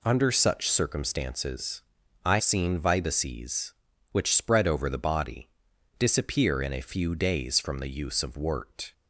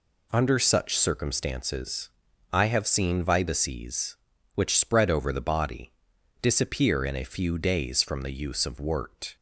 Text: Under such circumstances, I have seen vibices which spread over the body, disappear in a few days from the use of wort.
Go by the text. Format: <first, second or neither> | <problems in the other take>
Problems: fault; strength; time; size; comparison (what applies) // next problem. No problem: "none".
second | skips "have"; at 2.3 s